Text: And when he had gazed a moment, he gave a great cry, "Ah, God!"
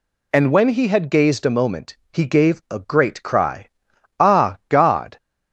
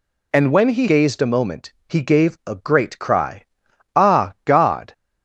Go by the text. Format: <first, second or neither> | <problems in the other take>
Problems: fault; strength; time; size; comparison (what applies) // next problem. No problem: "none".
first | skips "had"; at 0.8 s